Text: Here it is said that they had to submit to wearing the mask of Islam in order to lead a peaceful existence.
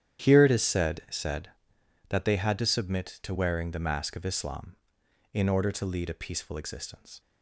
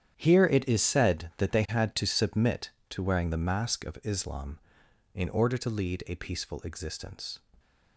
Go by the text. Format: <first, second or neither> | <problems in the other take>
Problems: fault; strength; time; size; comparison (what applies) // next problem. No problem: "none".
second | starts louder than the rest; strong; until 1.2 s; 10.5 dB; strong in the second // says "said" twice; at 1.0 s